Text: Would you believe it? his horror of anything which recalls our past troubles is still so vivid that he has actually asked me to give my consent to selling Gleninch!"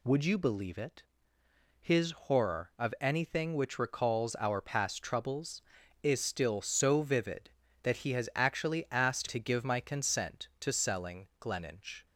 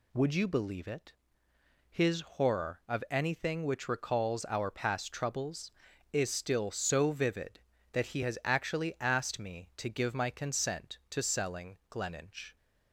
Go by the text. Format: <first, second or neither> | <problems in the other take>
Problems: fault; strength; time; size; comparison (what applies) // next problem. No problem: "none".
second | skips "me"; at 9.2 s